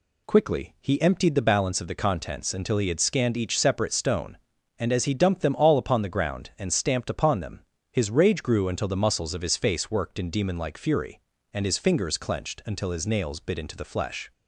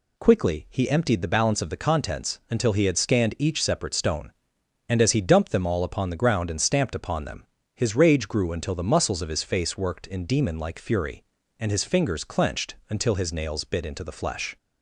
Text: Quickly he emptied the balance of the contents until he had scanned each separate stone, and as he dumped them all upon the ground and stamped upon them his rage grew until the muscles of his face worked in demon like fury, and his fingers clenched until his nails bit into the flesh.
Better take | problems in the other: neither | pauses between "them" and "his"; slight; the same in both

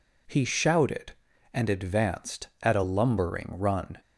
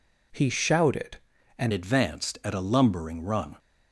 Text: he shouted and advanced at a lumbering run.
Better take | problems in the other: first | changes voice at "advanced"; from 1.7 s on; 1.8 s long

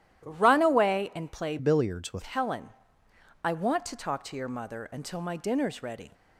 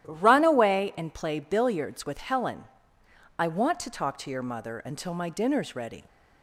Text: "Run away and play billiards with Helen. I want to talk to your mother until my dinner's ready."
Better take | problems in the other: second | starts louder than the rest; strong; until 1.2 s; 12 dB; strong in the second // changes voice from "billiards" to "with"; from 1.5 to 2.2 s; 0.7 s long

